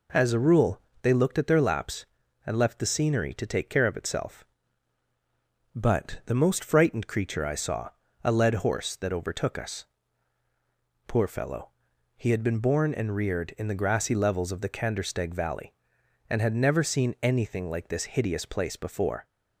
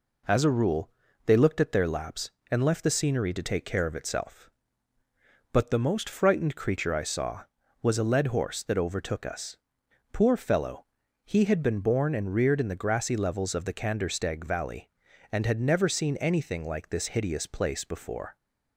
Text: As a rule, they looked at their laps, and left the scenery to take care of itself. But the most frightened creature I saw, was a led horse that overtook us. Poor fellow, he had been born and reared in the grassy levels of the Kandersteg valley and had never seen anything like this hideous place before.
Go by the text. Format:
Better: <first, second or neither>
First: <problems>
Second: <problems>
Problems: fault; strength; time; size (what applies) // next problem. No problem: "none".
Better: second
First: skips "was"; at 8.0 s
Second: none